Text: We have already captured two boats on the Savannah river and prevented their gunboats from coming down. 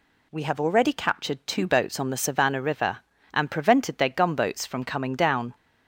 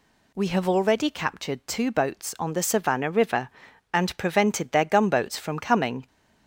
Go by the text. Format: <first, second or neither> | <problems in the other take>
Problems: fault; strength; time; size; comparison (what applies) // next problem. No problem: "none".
first | stops before "down"; at 6.0 s